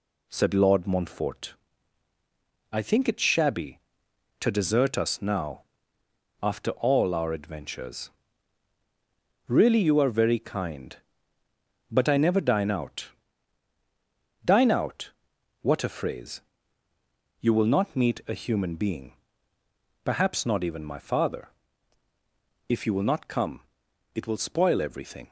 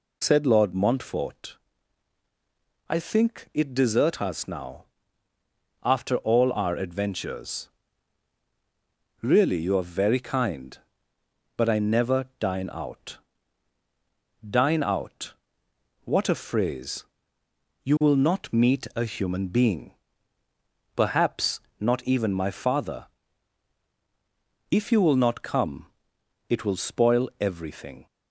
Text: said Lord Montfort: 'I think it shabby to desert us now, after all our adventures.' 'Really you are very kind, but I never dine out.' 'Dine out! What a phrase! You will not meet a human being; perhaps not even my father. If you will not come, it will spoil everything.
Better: first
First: none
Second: skips "shabby to"; at 3.7 s // pauses between "perhaps" and "not"; slight; at 21.5 s; 0.20 s long

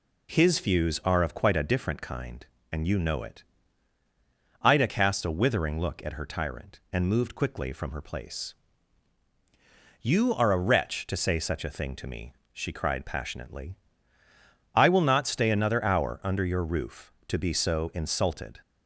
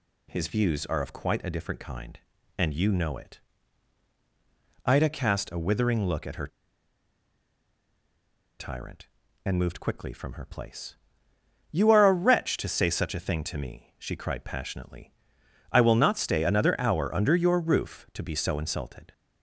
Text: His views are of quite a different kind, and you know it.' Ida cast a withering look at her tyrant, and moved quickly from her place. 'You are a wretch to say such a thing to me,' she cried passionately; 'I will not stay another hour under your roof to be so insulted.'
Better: first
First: none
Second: pauses between "her" and "tyrant"; strong; at 6.4 s; 2.1 s long

